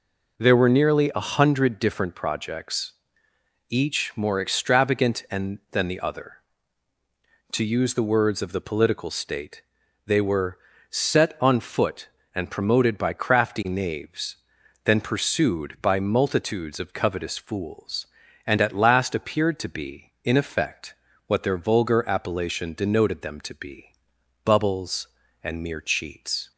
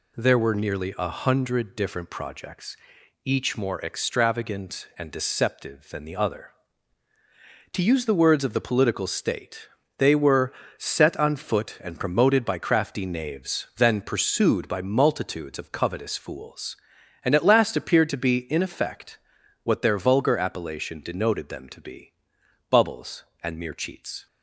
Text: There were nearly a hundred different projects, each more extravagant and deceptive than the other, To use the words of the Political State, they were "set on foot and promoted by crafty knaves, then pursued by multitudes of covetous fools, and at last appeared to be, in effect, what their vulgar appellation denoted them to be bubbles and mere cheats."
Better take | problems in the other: second | skips "deceptive"; at 5.6 s // pauses between "were" and "set"; slight; at 10.5 s; 0.32 s long; slight in the second // pauses between "be" and "bubbles"; noticeable; at 23.9 s; 0.54 s long; noticeable in the second

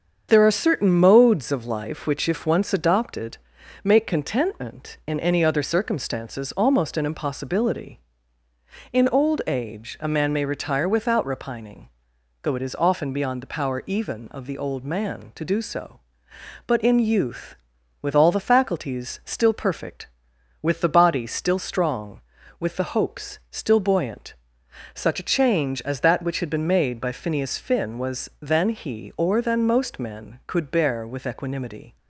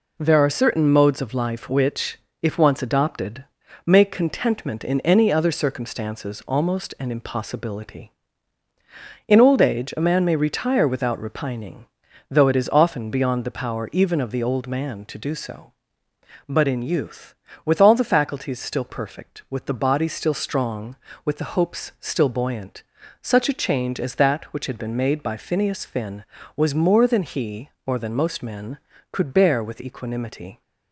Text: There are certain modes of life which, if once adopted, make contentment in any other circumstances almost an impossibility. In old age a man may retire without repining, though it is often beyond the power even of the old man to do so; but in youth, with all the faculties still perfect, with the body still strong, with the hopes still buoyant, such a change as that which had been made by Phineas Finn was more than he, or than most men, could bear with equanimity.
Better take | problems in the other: second | starts louder than the rest; strong; until 1.3 s; 7 dB // skips "more"; at 28.3 s

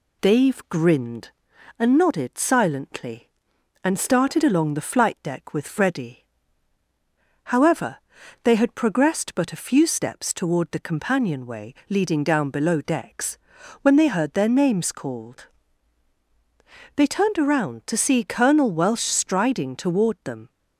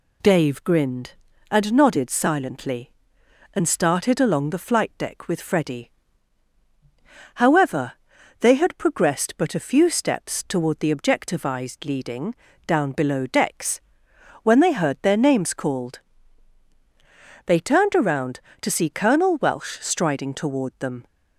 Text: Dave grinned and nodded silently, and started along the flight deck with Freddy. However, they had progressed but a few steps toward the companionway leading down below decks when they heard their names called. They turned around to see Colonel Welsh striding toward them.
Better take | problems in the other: first | says "objectivized" for "companionway"; at 10.9 s // pauses between "leading" and "down"; slight; at 12.3 s; 0.32 s long // pauses between "decks" and "when"; noticeable; at 13.8 s; 0.62 s long; also in the first

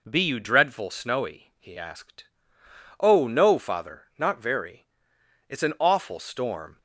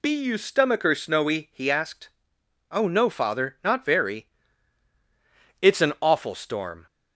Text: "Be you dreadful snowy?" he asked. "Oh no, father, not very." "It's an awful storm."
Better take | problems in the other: first | says "stomacher" for "dreadful"; at 0.3 s

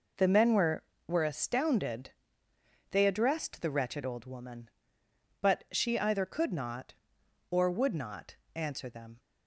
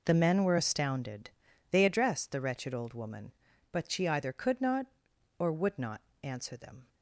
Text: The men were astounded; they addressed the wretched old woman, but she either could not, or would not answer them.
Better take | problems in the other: second | says "were" twice; at 1.0 s // pauses between "not" and "answer"; slight; at 8.3 s; 0.20 s long; slight in the second

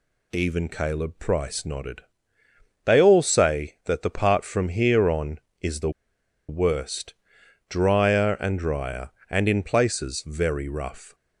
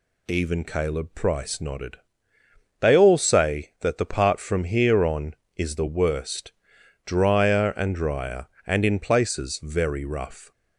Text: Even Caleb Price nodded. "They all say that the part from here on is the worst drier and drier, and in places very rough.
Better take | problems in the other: second | pauses between "the" and "worst"; noticeable; at 5.9 s; 0.58 s long // pauses between "worst" and "drier"; noticeable; at 7.1 s; 0.54 s long; noticeable in the second

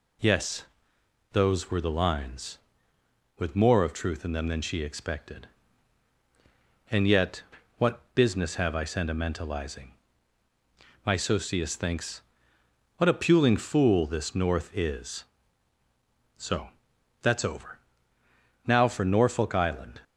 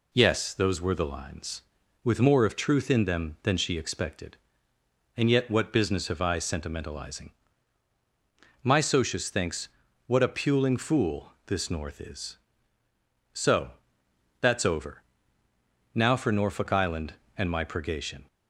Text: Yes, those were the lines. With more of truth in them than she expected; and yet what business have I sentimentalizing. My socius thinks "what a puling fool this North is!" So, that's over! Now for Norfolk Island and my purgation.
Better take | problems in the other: second | pauses between "yet" and "what"; slight; at 7.4 s; 0.34 s long // pauses between "thinks" and "what"; noticeable; at 12.2 s; 0.76 s long; slight in the second // stops before "and my purgation"; at 20.0 s

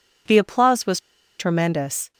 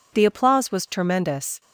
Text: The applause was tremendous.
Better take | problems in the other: second | pauses between "was" and "tremendous"; at 0.9 s; 0.39 s long

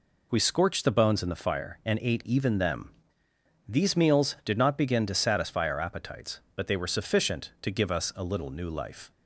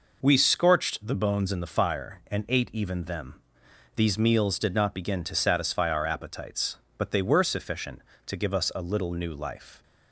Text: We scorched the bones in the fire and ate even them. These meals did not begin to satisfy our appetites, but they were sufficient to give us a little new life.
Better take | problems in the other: neither | none

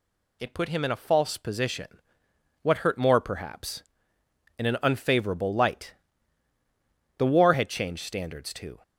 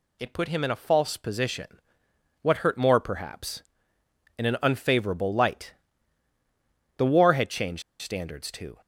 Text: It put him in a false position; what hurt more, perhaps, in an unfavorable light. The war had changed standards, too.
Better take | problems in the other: first | pauses between "changed" and "standards"; slight; at 7.8 s; 0.19 s long

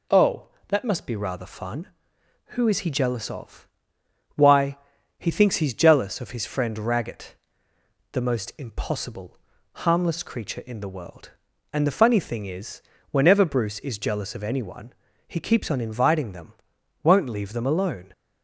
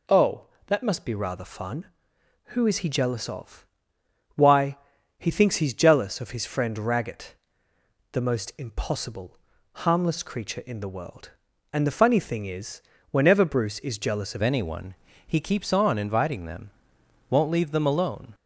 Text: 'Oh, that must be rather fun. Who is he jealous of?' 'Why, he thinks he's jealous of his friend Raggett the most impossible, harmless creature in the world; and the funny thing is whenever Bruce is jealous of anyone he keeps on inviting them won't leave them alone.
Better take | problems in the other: first | pauses between "Raggett" and "the"; noticeable; at 7.3 s; 0.78 s long; noticeable in the first // pauses between "is" and "whenever"; slight; at 12.8 s; 0.30 s long; slight in the first // changes voice at "anyone"; from 14.4 s on; 3.9 s long // pauses between "anyone" and "he"; slight; at 14.9 s; 0.30 s long; slight in the first // pauses between "them" and "won't"; noticeable; at 16.6 s; 0.62 s long; noticeable in the first

